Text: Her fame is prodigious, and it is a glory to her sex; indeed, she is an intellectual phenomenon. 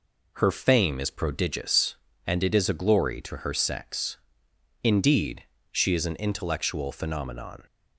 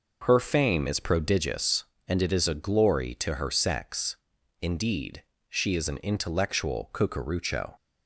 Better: first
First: none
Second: says "cucurucho" for "phenomenon"; at 6.9 s

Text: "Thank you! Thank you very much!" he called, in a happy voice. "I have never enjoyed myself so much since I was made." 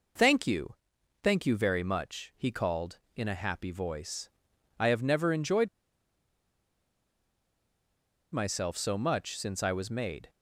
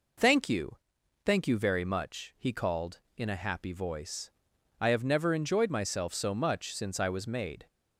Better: second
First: pauses between "enjoyed" and "myself"; strong; at 5.6 s; 2.6 s long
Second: none

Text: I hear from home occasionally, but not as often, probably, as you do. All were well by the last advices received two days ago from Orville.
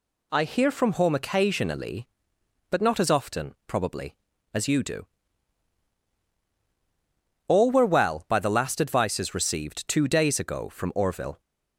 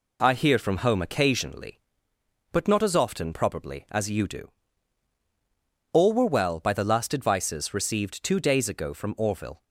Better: neither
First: none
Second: none

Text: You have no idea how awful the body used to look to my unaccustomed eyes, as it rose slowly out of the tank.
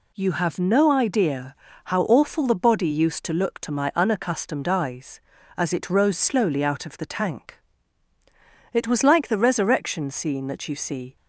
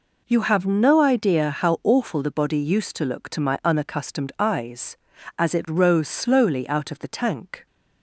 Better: second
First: pauses between "idea" and "how"; slight; at 1.5 s; 0.30 s long // goes on to say "It was like the resurrection scene that you see"; strong; from 8.7 s on; 2.4 s long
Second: none

